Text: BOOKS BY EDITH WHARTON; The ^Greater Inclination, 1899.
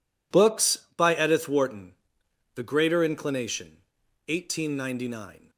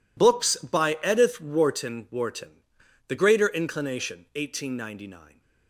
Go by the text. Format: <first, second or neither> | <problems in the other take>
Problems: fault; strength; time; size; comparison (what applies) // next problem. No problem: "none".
first | says "WHARTON" twice; at 2.0 s